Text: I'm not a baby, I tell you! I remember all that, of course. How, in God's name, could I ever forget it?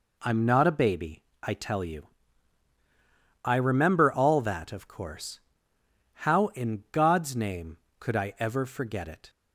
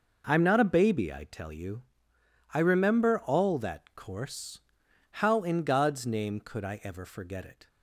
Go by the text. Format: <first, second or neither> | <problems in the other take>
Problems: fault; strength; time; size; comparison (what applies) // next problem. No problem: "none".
first | skips "of"; at 3.9 s